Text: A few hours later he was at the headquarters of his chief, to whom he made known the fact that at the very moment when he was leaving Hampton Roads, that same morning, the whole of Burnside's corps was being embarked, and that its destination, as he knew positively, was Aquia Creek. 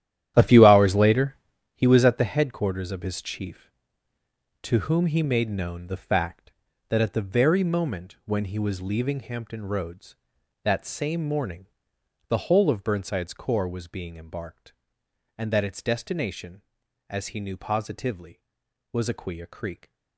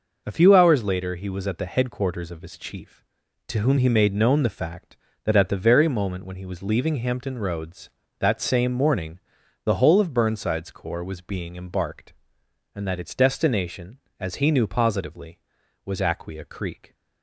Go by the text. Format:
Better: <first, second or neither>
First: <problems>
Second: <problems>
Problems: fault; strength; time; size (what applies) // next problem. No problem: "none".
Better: second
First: starts louder than the rest; strong; until 1.9 s; 11.5 dB // pauses between "later" and "he"; at 1.3 s; 0.40 s long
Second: none